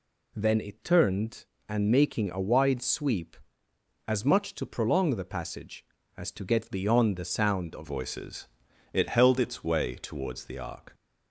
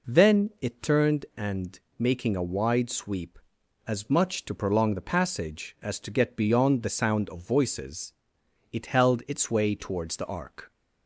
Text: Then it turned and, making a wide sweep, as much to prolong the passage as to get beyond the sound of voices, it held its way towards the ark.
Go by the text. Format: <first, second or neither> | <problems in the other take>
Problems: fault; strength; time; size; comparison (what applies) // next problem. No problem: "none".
second | changes voice at "voices"; from 7.8 s on; 3.1 s long